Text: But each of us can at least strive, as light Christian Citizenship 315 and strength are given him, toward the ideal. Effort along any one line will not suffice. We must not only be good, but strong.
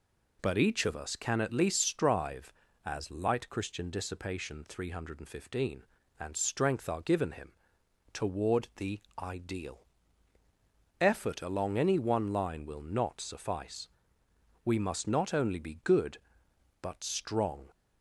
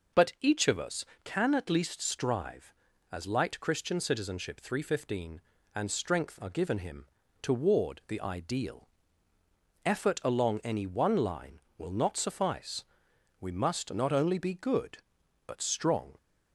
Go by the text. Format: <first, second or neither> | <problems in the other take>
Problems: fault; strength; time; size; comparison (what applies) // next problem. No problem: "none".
second | says "Dissipation" for "Citizenship"; at 3.9 s // pauses between "the" and "ideal"; slight; at 9.0 s; 0.18 s long